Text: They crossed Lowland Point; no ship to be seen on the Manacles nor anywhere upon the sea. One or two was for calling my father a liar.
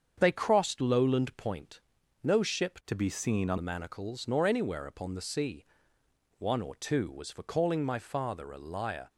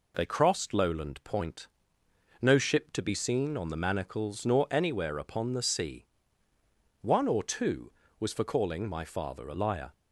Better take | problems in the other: second | starts louder than the rest; strong; until 1.1 s; 7.5 dB // changes voice from "to" to "on"; from 2.8 to 3.5 s; 0.7 s long

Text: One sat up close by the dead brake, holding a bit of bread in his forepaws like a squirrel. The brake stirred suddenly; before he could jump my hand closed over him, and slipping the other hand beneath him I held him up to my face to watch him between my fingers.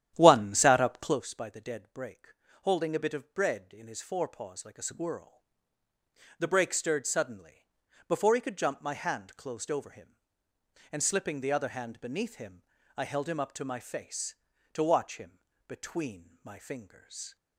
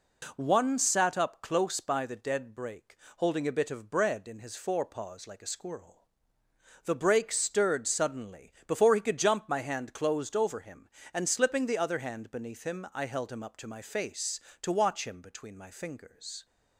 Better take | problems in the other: second | starts louder than the rest; strong; until 1.3 s; 11 dB // pauses between "him" and "I"; slight; at 12.6 s; 0.34 s long // pauses between "him" and "between"; slight; at 15.3 s; 0.28 s long

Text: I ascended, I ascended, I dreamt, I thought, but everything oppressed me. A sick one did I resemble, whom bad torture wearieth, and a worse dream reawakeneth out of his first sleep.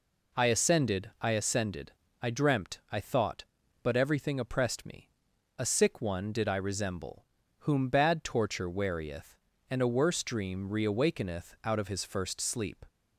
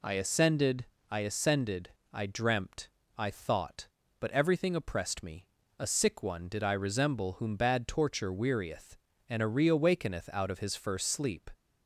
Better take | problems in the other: first | skips "worse dream"; at 9.4 s

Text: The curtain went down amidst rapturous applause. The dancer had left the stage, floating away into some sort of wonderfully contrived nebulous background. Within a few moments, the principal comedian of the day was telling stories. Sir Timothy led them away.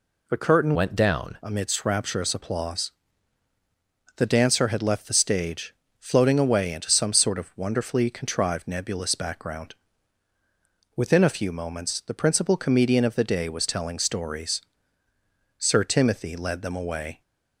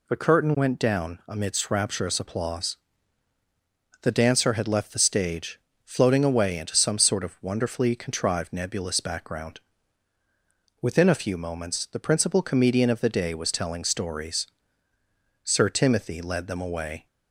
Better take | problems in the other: second | changes voice from "went" to "down"; from 0.7 to 1.3 s; 0.6 s long

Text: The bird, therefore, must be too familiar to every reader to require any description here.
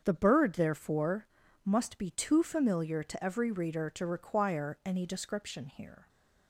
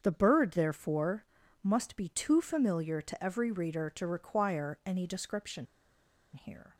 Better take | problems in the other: first | starts louder than the rest; strong; until 1.0 s; 7.5 dB; strong in the first // pauses between "description" and "here"; noticeable; at 5.6 s; 0.68 s long

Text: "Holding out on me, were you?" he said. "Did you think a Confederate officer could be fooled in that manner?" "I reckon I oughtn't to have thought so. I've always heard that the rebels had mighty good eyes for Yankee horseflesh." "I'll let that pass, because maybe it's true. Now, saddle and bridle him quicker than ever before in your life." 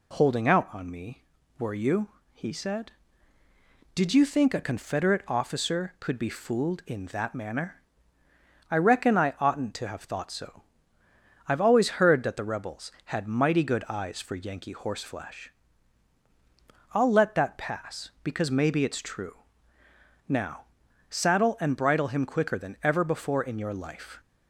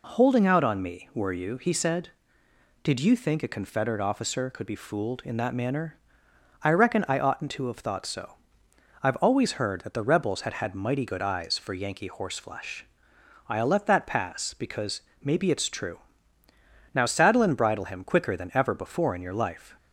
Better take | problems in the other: first | says "had" twice; at 10.5 s // pauses between "because" and "maybe"; slight; at 14.9 s; 0.22 s long

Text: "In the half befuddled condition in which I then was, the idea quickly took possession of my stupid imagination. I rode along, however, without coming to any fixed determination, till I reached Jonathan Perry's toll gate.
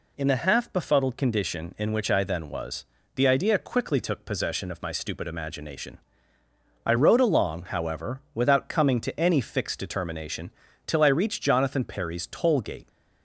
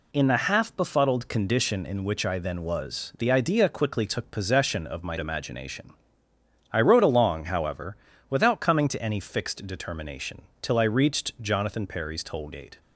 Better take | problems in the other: first | skips "stupid"; at 5.1 s

